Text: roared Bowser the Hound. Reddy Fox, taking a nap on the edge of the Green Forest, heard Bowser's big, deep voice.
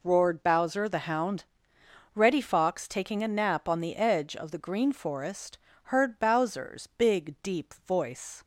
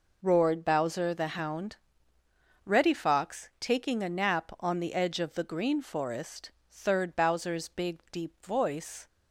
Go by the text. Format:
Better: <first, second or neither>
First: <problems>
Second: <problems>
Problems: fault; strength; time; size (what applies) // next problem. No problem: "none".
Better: first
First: none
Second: says "third" for "heard"; at 6.7 s